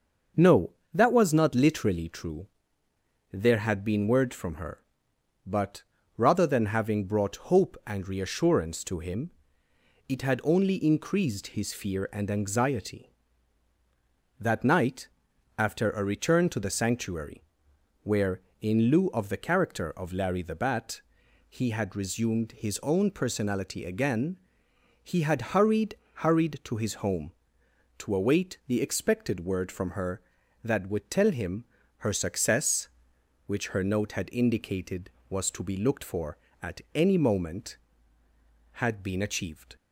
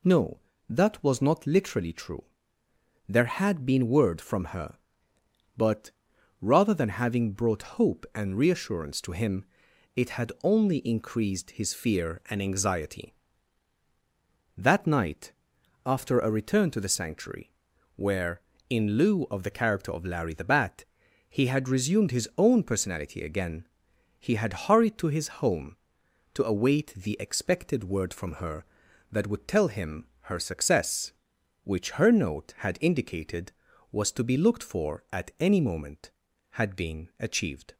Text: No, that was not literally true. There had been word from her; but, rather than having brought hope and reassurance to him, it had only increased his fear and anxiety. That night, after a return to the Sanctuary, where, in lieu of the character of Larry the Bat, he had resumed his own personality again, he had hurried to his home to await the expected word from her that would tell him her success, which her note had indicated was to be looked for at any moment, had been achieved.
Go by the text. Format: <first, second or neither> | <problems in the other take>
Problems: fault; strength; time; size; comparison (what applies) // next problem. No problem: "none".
second | starts louder than the rest; until 1.6 s; 6 dB // says "hurried" twice; at 26.1 s // pauses between "him" and "her"; slight; at 31.6 s; 0.32 s long